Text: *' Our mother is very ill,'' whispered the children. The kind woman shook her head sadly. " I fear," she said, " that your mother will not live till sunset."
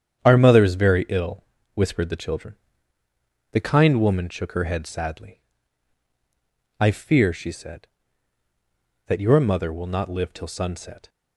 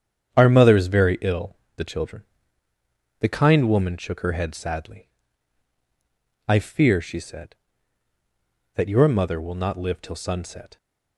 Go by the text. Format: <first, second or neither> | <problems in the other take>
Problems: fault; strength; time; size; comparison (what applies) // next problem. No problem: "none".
first | starts louder than the rest; strong; until 1.3 s; 10 dB; strong in the first // skips "whispered"; at 1.6 s